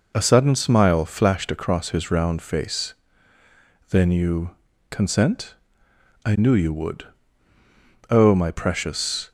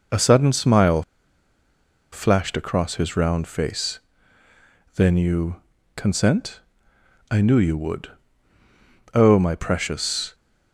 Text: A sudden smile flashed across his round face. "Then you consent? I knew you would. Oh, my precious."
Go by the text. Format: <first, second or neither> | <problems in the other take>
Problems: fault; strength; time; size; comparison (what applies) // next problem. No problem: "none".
first | pauses between "smile" and "flashed"; at 1.0 s; 1.1 s long // pauses between "you" and "consent"; slight; at 5.6 s; 0.34 s long; slight in the first